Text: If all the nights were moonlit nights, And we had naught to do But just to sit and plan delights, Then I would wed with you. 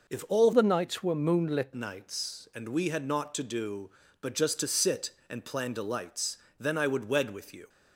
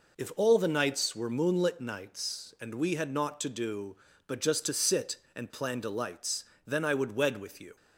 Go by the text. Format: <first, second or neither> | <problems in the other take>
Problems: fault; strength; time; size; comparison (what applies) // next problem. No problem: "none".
second | changes voice from "the" to "moonlit"; from 0.5 to 1.7 s; 1.2 s long